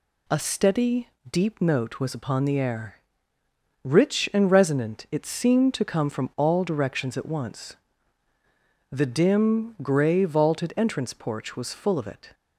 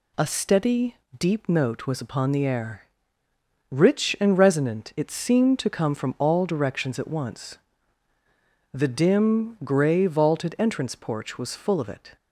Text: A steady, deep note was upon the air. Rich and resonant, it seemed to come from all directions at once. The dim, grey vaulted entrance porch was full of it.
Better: neither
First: none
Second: none

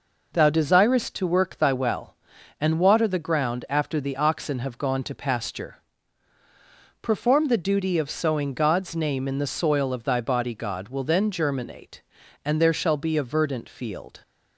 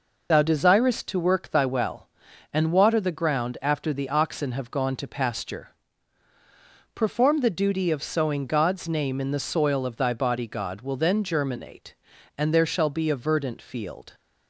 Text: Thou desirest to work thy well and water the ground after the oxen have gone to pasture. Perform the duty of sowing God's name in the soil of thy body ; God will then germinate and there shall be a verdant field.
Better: first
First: none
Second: loses the start of "Thou"; at 0.3 s; 35 ms

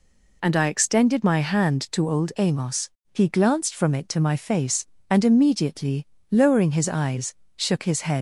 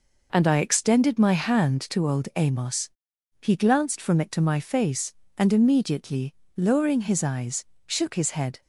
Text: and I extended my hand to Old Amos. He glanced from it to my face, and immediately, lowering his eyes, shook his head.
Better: second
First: leaves "head" unfinished; at 8.1 s; 105 ms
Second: none

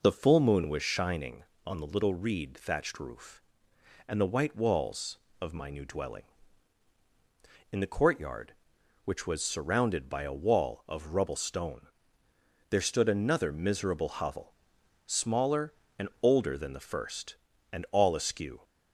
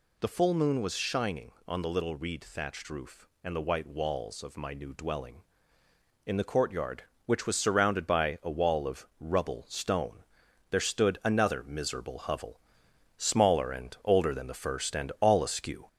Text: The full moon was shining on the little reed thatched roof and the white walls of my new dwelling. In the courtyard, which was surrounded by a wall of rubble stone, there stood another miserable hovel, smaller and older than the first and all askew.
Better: first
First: none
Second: gets louder; slight; throughout; 3 dB

